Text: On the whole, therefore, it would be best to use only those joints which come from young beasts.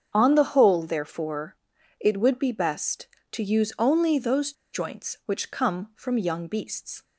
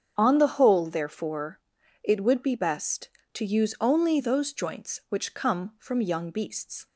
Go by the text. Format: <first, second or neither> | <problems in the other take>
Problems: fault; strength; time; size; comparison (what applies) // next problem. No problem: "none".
second | starts louder than the rest; strong; until 1.1 s; 8 dB; strong in the second // pauses between "those" and "joints"; slight; at 4.5 s; 0.20 s long